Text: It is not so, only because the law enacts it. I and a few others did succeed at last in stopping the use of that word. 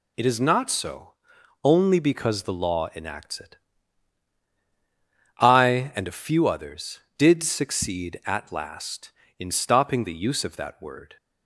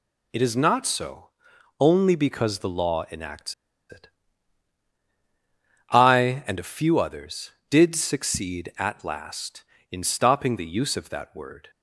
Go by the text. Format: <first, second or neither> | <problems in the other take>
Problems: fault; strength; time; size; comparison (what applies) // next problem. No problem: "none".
first | pauses between "enacts" and "it"; at 3.5 s; 0.36 s long